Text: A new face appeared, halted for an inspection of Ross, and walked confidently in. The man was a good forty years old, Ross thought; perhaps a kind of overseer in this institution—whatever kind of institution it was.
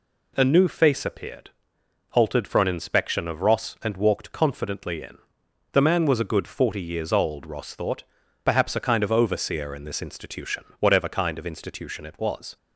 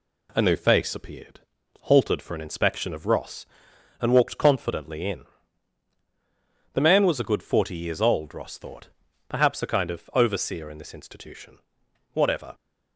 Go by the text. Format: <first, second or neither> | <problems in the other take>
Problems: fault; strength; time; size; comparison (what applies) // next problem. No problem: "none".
first | stops before "kind of institution it was"; at 12.5 s